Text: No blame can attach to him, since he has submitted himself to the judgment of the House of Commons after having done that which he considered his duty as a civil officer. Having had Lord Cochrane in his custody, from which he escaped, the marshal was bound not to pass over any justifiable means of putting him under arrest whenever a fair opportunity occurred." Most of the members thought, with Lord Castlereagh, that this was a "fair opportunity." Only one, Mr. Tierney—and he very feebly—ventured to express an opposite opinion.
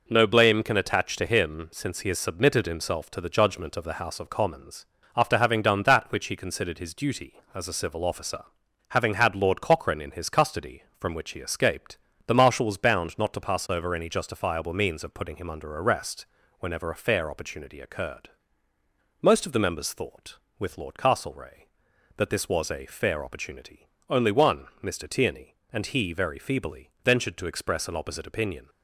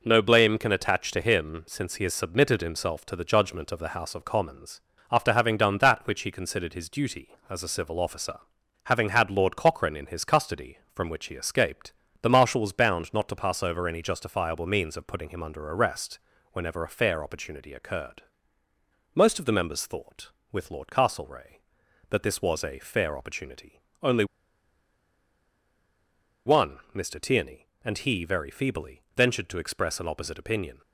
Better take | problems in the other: first | pauses between "Commons" and "after"; slight; at 4.8 s; 0.32 s long; slight in the first // pauses between "arrest" and "whenever"; slight; at 16.2 s; 0.32 s long; slight in the first // pauses between "Only" and "one"; strong; at 24.2 s; 2.2 s long

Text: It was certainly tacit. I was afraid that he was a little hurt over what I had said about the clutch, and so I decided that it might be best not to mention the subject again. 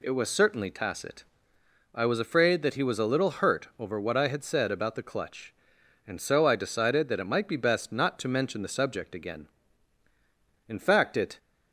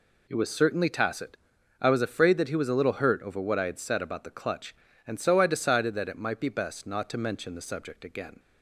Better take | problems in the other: second | goes on to say "In fact it"; noticeable; from 10.6 s on; 0.70 s long

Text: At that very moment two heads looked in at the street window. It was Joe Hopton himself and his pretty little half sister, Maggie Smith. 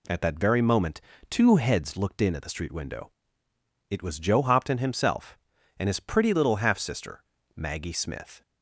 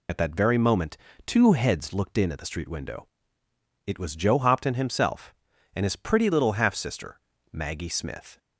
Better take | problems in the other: first | loses the start of "At"; at 0.0 s; 75 ms // pauses between "moment" and "two"; slight; at 0.9 s; 0.30 s long; slight in the first

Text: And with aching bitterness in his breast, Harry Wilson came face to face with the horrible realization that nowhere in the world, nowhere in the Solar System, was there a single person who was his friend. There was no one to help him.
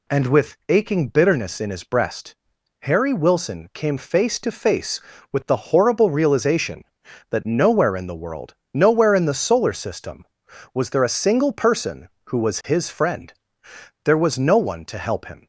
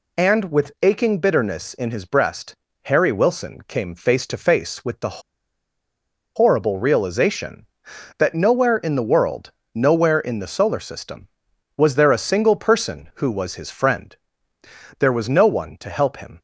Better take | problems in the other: first | pauses between "the" and "horrible"; at 5.2 s; 1.1 s long

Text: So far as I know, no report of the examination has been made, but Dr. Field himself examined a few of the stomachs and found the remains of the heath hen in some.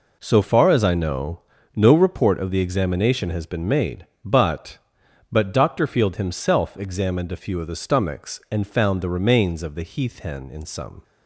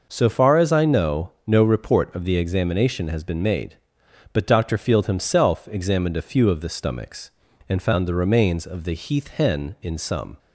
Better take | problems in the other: second | says "but" twice; at 5.3 s

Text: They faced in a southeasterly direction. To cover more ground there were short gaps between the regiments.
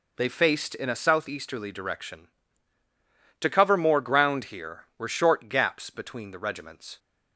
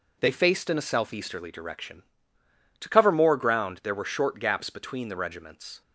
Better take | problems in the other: second | says "here" for "there"; at 4.4 s

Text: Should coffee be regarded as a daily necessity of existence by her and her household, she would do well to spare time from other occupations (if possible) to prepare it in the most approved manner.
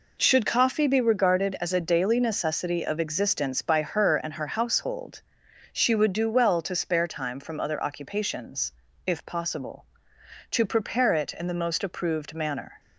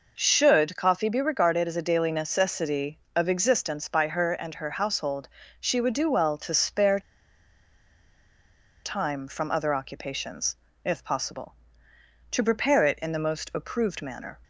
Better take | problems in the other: first | pauses between "spare" and "time"; strong; at 6.9 s; 1.8 s long

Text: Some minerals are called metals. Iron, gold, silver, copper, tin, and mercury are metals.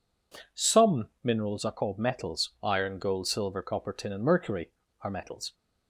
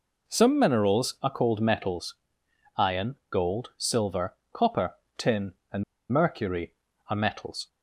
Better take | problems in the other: first | pauses between "and" and "mercury"; slight; at 5.8 s; 0.28 s long

